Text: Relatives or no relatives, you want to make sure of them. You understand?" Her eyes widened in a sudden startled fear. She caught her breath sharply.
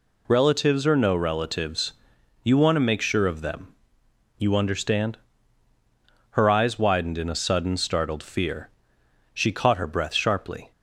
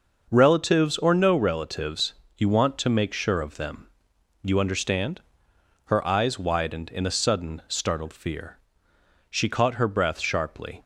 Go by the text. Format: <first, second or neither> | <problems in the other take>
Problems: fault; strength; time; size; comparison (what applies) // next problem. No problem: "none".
neither | none